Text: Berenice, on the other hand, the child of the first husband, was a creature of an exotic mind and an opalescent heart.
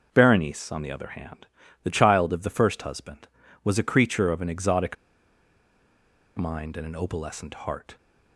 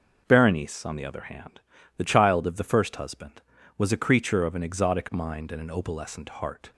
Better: second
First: pauses between "exotic" and "mind"; strong; at 4.9 s; 1.4 s long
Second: none

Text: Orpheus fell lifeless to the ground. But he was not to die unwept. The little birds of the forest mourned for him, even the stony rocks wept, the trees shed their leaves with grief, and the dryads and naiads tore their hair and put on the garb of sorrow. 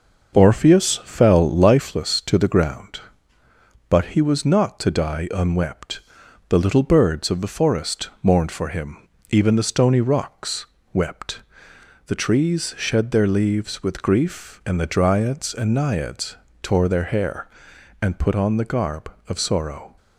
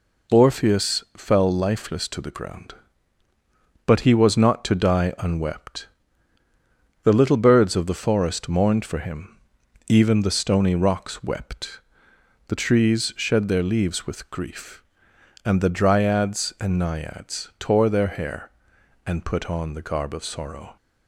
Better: second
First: starts louder than the rest; noticeable; until 1.9 s; 6 dB // pauses between "rocks" and "wept"; slight; at 10.6 s; 0.26 s long // pauses between "naiads" and "tore"; slight; at 16.3 s; 0.26 s long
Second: none

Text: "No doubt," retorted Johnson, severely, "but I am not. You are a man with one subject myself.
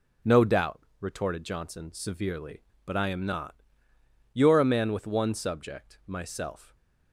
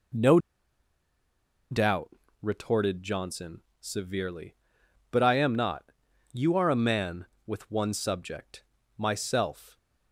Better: first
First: none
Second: pauses between "No" and "doubt"; strong; at 0.3 s; 1.3 s long // pauses between "subject" and "myself"; slight; at 8.6 s; 0.34 s long

